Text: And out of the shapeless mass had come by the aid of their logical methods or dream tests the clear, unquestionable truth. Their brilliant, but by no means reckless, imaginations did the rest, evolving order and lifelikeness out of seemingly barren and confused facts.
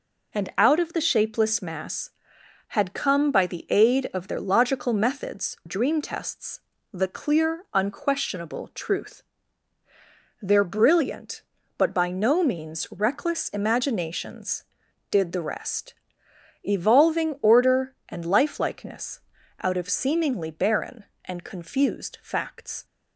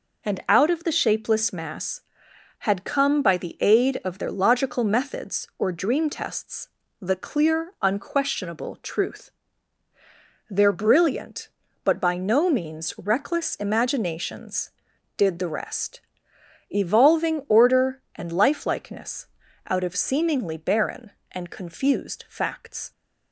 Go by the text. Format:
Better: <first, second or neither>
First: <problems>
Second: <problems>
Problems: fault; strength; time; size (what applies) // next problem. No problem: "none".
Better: second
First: skips "or"; at 5.6 s // pauses between "tests" and "the"; slight; at 6.5 s; 0.34 s long // pauses between "lifelikeness" and "out"; at 19.2 s; 0.40 s long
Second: pauses between "tests" and "the"; slight; at 6.6 s; 0.34 s long // pauses between "lifelikeness" and "out"; at 19.2 s; 0.40 s long